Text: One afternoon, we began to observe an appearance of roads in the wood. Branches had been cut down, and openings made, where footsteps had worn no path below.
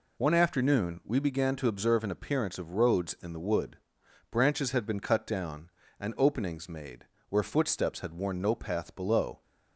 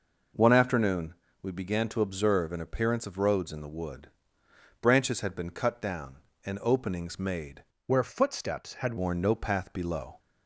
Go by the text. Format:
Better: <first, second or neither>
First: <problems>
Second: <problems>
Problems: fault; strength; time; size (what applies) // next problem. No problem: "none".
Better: first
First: none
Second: changes voice from "where" to "had"; from 7.8 to 8.9 s; 1.1 s long